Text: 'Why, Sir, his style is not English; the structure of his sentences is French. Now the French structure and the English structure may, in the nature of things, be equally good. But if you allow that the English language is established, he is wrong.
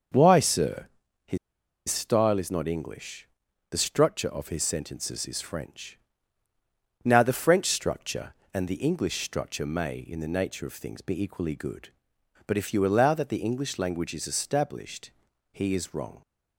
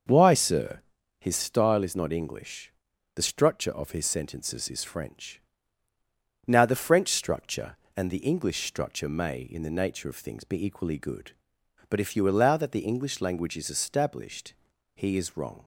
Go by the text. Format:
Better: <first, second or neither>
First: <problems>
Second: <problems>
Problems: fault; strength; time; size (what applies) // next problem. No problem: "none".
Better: second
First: starts louder than the rest; until 2.0 s; 6 dB // pauses between "his" and "style"; noticeable; at 1.3 s; 0.51 s long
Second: starts louder than the rest; until 1.4 s; 6 dB